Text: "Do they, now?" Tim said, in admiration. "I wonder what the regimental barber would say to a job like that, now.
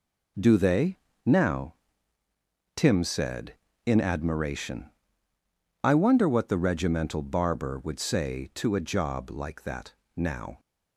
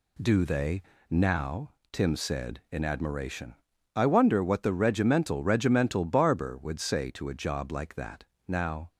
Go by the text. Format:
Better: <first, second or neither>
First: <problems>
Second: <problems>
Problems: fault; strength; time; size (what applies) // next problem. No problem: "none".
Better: first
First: none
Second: says "regimental" twice; at 5.4 s